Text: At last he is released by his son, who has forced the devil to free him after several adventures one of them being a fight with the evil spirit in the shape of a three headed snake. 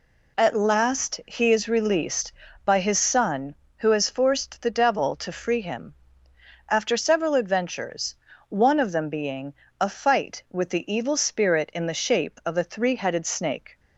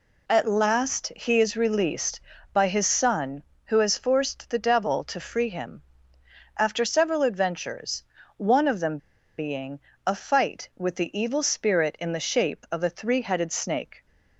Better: first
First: pauses between "him" and "after"; noticeable; at 5.9 s; 0.74 s long // pauses between "adventures" and "one"; slight; at 8.1 s; 0.34 s long // pauses between "being" and "a"; slight; at 9.5 s; 0.26 s long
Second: pauses between "him" and "after"; noticeable; at 5.8 s; 0.74 s long // pauses between "adventures" and "one"; slight; at 8.0 s; 0.34 s long // pauses between "them" and "being"; at 8.9 s; 0.40 s long // pauses between "being" and "a"; slight; at 9.7 s; 0.26 s long

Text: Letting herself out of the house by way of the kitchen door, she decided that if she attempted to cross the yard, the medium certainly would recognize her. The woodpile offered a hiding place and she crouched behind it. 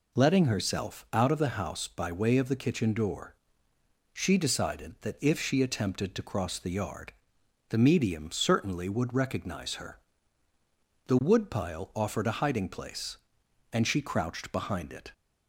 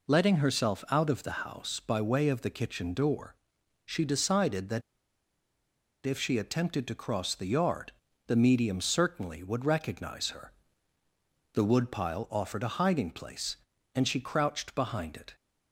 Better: first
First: none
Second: pauses between "that" and "if"; at 4.8 s; 1.2 s long

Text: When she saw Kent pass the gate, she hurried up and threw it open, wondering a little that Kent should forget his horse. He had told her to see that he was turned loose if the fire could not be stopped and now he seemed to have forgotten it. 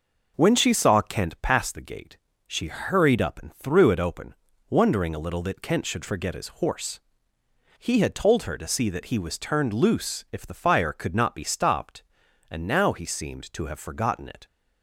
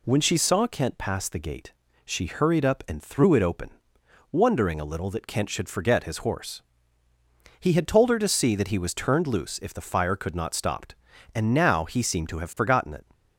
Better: first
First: none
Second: skips "be"; at 10.5 s

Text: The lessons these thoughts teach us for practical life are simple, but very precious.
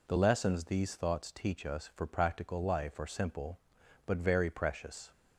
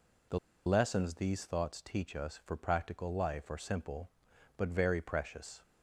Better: first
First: none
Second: pauses between "The" and "lessons"; slight; at 0.3 s; 0.27 s long

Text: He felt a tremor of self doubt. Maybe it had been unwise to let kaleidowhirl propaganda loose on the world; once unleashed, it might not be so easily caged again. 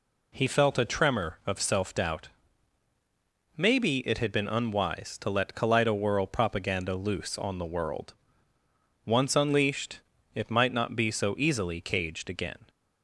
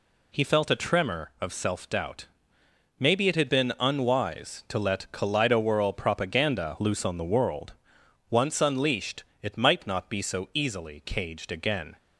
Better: neither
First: none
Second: none

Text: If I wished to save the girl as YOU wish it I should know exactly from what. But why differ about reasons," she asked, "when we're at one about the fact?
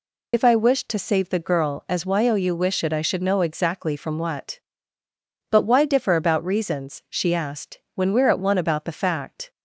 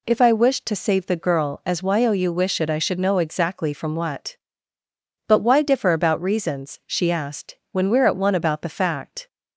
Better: second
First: loses the start of "If"; at 0.3 s; 55 ms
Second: none

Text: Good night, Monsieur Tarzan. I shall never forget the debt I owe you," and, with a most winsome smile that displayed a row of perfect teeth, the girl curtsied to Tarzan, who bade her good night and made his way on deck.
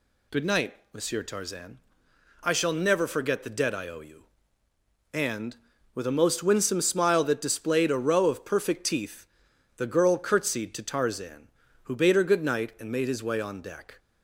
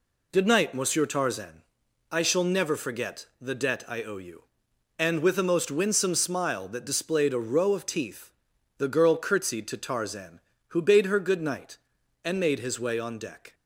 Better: first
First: none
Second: pauses between "forget" and "the"; slight; at 3.2 s; 0.16 s long // skips "perfect"; at 7.8 s

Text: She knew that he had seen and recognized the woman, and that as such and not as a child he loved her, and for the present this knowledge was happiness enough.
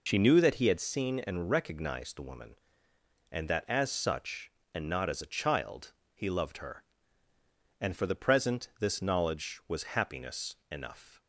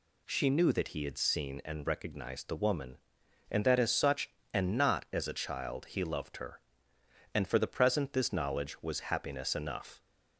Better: second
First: loses the start of "She"; at 0.0 s; 45 ms // pauses between "child" and "he"; slight; at 5.9 s; 0.20 s long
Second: none

